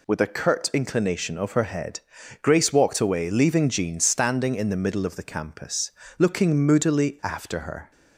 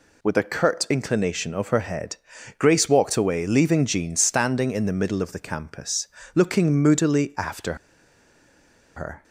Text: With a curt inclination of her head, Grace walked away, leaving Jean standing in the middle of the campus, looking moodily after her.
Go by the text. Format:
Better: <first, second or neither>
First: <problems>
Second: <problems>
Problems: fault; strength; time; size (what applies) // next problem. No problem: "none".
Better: first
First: none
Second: pauses between "after" and "her"; at 7.7 s; 1.2 s long